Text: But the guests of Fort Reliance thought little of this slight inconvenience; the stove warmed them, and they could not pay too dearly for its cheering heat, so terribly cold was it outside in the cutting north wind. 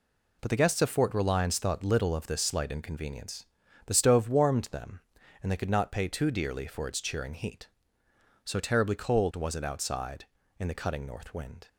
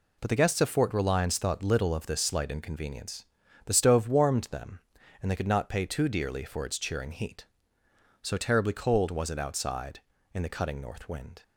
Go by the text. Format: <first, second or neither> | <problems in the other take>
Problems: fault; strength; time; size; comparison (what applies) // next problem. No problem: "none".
neither | none